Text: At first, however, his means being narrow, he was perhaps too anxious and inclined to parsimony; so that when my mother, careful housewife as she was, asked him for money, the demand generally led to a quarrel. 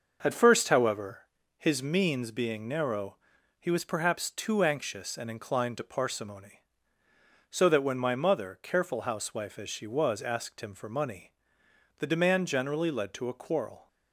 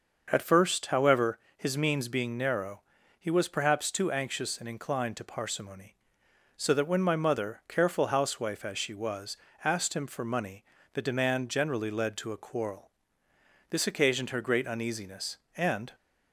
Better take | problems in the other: first | starts louder than the rest; until 1.3 s; 6 dB; noticeable in the first // goes on to say "This occasioned her great uneasiness and"; strong; from 13.7 s on; 2.2 s long

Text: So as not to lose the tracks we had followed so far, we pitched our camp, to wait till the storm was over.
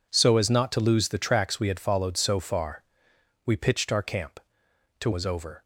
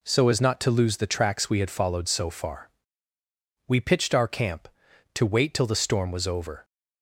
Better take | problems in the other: second | skips "wait till the storm"; at 5.1 s

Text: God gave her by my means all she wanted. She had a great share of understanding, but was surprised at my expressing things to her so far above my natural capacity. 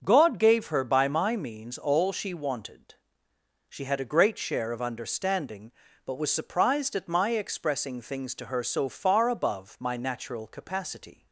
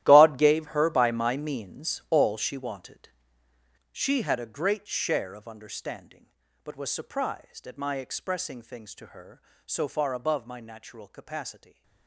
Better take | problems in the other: first | gets quieter; strong; throughout; 15.5 dB // starts louder than the rest; strong; until 1.0 s; 13.5 dB; also in the first

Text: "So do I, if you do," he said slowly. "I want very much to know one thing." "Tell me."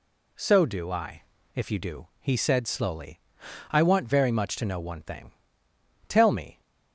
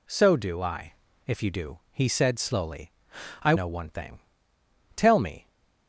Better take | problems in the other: first | skips "want very much to"; at 3.5 s

